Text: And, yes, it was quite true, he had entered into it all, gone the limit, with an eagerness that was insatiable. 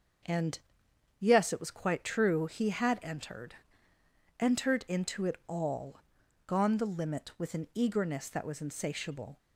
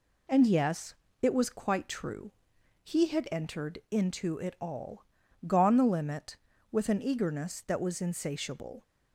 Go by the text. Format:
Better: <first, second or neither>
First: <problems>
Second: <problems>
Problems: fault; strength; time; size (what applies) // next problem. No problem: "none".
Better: second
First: starts louder than the rest; until 1.8 s; 7 dB // says "entered" twice; at 4.3 s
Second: none